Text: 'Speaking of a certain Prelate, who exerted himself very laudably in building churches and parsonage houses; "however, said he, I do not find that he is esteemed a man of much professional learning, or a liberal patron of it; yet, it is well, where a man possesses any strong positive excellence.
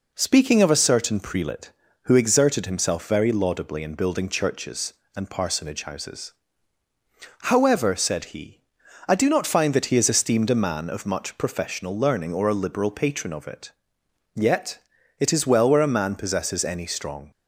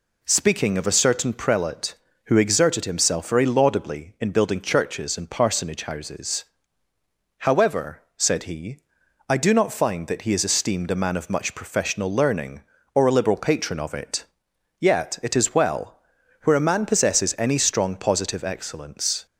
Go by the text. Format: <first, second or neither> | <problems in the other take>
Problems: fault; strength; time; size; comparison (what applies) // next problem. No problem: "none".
second | stops before "positive excellence"; at 17.3 s